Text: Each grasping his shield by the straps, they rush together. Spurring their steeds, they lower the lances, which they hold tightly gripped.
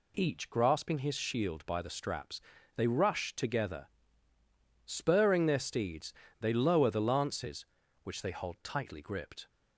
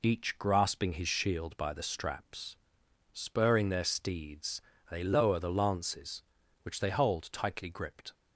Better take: first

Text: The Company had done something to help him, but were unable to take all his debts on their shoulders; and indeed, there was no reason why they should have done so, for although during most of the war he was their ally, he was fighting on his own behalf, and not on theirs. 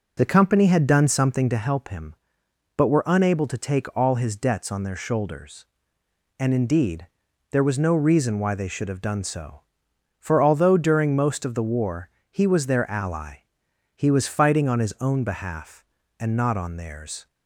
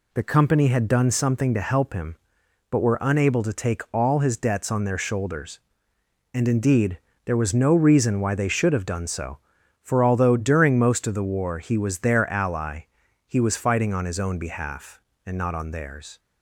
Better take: second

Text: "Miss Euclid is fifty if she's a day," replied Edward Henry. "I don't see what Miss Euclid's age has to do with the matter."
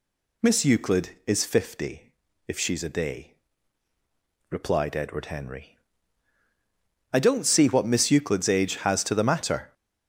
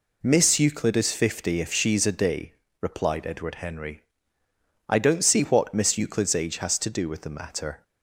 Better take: second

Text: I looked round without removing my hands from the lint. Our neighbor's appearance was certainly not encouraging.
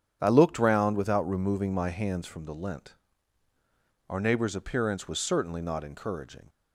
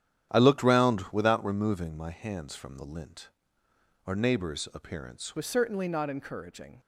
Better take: first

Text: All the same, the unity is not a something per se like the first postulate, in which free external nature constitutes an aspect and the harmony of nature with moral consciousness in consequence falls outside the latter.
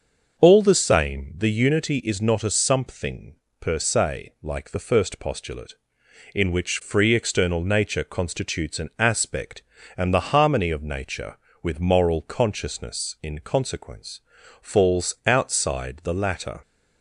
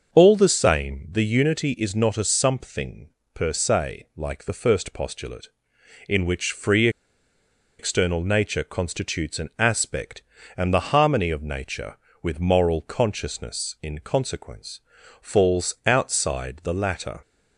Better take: first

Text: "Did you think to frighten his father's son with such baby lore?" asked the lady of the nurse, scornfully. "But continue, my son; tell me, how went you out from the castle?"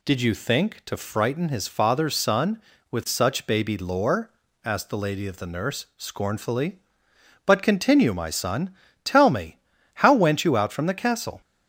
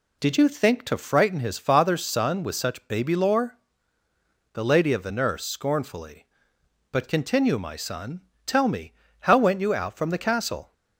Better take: first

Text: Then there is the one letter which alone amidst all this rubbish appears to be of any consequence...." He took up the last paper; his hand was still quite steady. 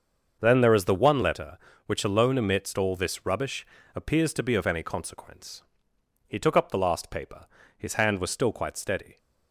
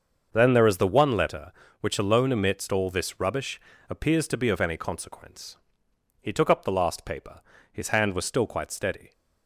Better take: neither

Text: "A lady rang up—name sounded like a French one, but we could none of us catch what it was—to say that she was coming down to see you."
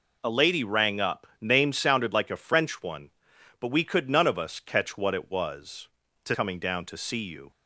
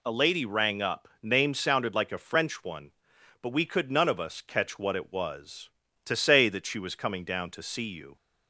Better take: second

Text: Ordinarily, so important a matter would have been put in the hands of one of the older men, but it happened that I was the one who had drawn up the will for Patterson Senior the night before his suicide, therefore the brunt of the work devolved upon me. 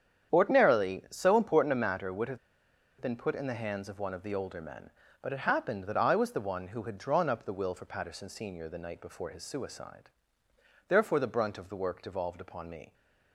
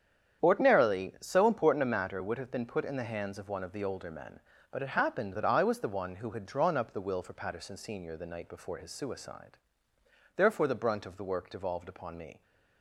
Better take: second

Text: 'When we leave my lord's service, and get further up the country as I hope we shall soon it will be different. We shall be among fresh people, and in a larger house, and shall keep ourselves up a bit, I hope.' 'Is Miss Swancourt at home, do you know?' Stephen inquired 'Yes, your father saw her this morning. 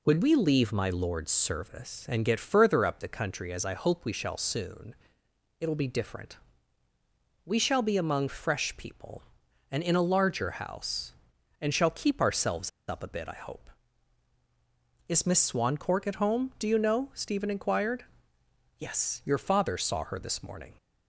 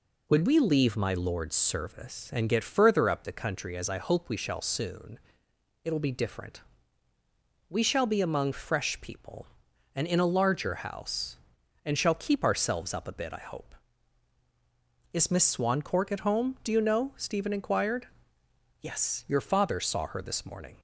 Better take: second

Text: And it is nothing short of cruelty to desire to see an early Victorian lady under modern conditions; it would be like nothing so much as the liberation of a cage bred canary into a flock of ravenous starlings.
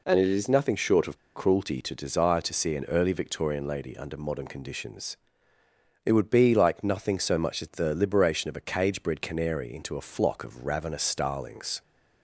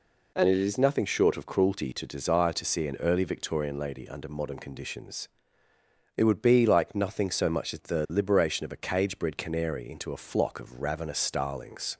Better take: second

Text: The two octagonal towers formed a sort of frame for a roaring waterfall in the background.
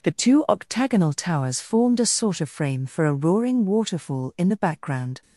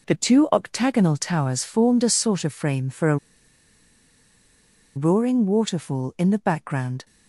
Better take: first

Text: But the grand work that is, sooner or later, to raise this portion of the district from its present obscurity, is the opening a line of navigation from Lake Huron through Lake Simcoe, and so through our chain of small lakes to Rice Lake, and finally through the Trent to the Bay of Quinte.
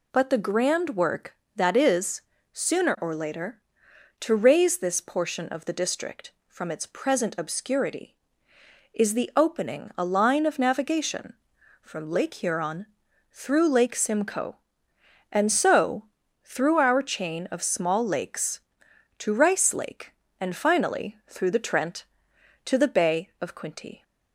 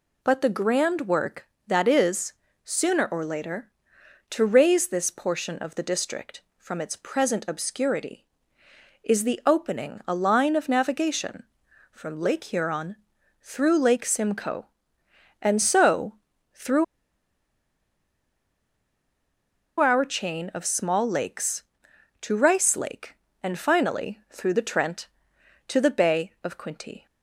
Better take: first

